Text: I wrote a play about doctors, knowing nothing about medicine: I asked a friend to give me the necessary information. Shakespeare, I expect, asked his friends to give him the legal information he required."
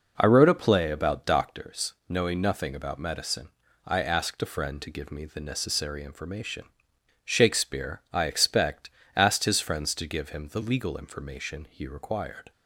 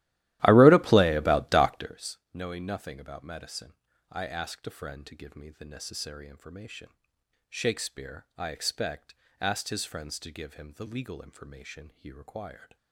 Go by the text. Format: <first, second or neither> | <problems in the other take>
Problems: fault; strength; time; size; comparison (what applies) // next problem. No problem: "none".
first | starts louder than the rest; strong; until 2.1 s; 15.5 dB